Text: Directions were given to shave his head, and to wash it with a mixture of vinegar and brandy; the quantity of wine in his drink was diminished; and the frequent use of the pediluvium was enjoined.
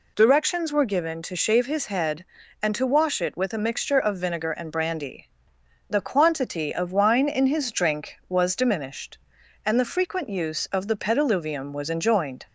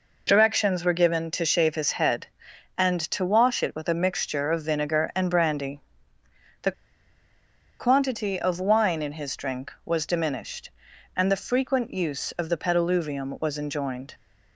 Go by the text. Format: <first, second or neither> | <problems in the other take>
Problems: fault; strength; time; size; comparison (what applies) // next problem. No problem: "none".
first | pauses between "the" and "quantity"; at 6.7 s; 1.0 s long